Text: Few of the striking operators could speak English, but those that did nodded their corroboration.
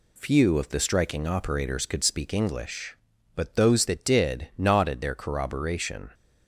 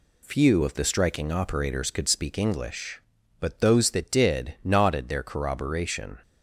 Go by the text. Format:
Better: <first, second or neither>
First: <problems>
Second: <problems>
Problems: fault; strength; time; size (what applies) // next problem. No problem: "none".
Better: neither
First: none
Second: none